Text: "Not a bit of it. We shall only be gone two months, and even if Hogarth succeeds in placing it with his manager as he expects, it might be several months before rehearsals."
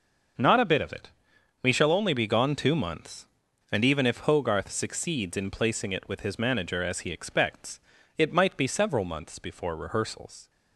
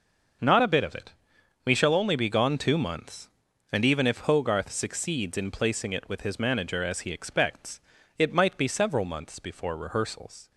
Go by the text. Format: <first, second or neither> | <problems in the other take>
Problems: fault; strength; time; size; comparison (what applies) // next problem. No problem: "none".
neither | starts louder than the rest; noticeable; the same in both